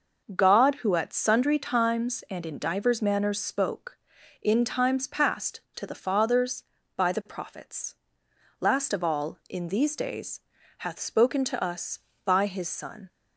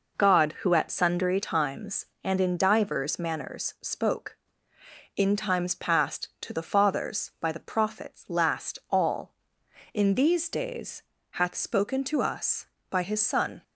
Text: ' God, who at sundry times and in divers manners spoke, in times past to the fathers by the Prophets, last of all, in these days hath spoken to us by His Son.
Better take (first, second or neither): first